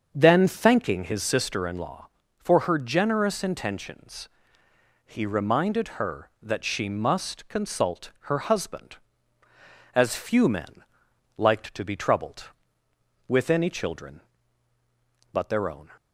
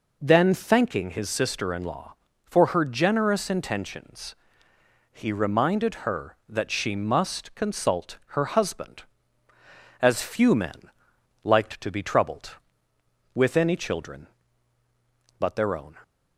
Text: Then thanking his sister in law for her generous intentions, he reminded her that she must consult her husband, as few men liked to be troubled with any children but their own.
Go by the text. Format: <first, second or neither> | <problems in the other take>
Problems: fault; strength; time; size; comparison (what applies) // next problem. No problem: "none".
second | starts louder than the rest; until 1.8 s; 7 dB // pauses between "men" and "liked"; noticeable; at 10.8 s; 0.54 s long; noticeable in the second